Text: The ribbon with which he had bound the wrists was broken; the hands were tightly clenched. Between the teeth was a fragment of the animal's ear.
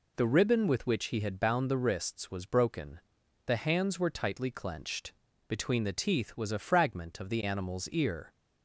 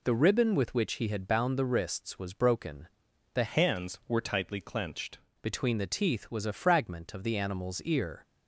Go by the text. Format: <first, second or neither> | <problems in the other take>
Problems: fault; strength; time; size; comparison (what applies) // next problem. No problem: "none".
first | changes voice from "hands" to "clenched"; from 3.4 to 5.1 s; 1.7 s long